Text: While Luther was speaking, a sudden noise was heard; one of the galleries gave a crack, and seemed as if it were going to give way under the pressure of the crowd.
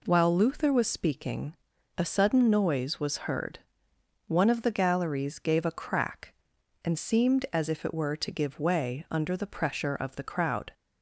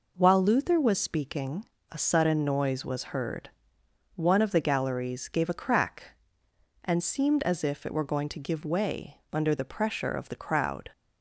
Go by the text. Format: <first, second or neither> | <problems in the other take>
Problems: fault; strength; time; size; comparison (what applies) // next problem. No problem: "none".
second | skips "going"; at 8.1 s